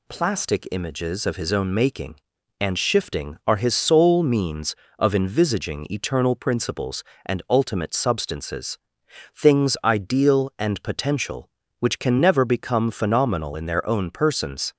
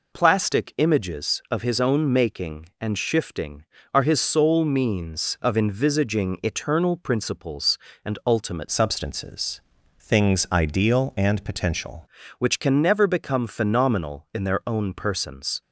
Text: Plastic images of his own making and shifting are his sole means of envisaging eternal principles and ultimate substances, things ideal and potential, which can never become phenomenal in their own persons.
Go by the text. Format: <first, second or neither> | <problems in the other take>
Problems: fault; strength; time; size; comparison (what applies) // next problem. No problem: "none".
first | changes voice from "substances" to "potential"; from 8.6 to 12.0 s; 3.4 s long